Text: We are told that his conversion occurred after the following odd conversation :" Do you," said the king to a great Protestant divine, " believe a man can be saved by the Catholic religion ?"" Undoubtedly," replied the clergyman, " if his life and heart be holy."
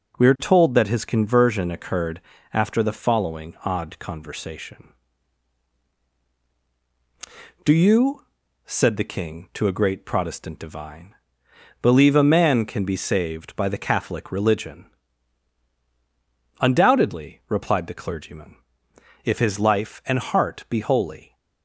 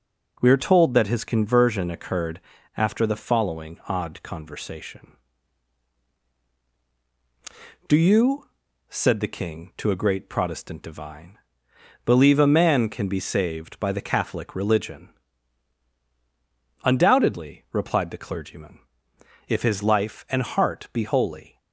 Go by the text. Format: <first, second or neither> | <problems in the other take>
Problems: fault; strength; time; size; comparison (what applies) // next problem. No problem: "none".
neither | starts louder than the rest; strong; the same in both // pauses between "occurred" and "after"; slight; the same in both